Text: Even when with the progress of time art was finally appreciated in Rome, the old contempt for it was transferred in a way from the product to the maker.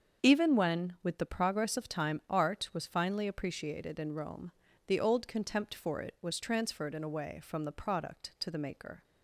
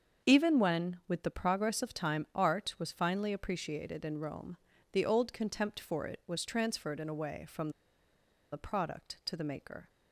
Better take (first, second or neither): first